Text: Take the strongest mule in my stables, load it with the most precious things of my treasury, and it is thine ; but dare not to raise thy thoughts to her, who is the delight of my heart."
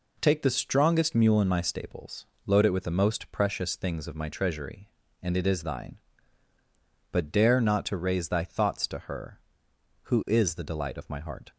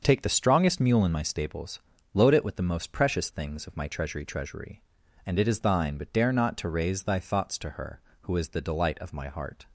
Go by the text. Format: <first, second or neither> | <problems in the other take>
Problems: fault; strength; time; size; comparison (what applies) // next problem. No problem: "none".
first | starts louder than the rest; until 1.0 s; 6.5 dB // says "treasury" twice; at 4.2 s